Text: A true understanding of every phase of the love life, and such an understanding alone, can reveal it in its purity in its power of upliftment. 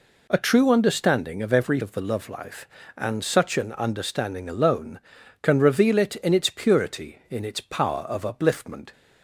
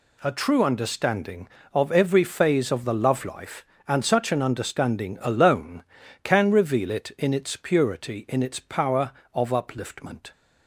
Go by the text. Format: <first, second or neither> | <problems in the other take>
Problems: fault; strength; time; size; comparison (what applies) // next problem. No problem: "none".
second | skips "phase"; at 1.7 s